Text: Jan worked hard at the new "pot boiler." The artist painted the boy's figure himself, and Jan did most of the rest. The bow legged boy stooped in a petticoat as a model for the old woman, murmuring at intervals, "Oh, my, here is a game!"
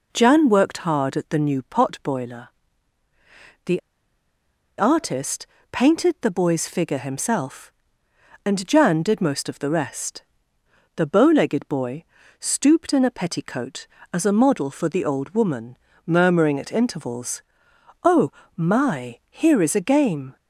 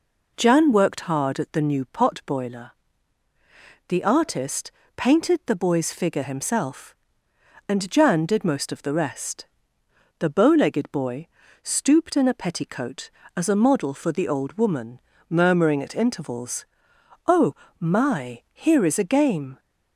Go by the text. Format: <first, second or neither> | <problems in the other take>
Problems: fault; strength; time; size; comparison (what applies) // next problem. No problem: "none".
second | pauses between "The" and "artist"; at 3.7 s; 0.98 s long // pauses between "artist" and "painted"; slight; at 5.4 s; 0.26 s long; slight in the second // pauses between "boy" and "stooped"; slight; at 12.0 s; 0.36 s long; slight in the second